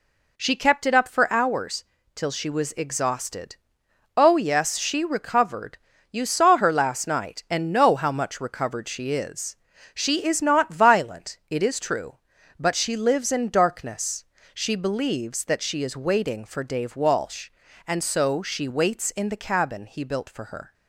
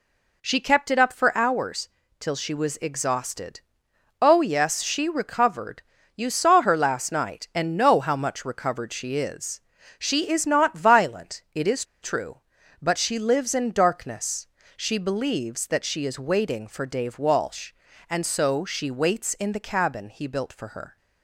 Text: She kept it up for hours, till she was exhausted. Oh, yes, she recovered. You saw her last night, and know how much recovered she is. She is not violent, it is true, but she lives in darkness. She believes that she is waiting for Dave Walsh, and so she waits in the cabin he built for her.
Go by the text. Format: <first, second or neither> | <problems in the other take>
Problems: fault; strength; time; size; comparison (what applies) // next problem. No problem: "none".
first | pauses between "is" and "true"; slight; at 11.8 s; 0.18 s long